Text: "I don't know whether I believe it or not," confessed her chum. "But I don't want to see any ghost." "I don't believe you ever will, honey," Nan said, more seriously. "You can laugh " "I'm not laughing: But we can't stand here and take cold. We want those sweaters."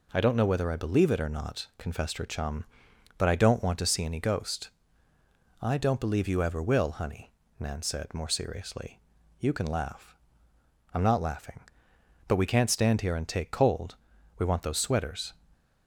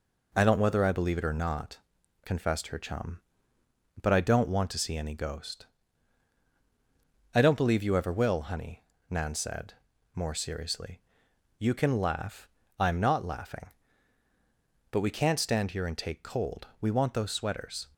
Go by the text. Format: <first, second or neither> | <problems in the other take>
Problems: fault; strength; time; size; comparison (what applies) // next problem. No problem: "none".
first | skips "know"; at 0.5 s